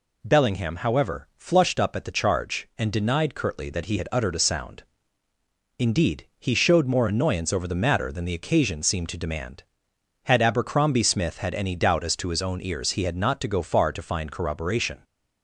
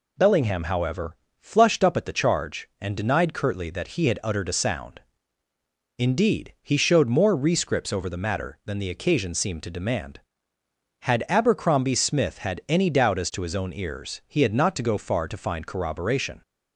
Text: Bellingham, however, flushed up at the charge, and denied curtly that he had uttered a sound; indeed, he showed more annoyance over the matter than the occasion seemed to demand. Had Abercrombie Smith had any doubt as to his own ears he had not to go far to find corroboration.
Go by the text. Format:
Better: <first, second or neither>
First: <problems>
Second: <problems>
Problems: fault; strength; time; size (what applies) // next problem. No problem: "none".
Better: first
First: none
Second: says "rescripts" for "annoyance"; at 7.3 s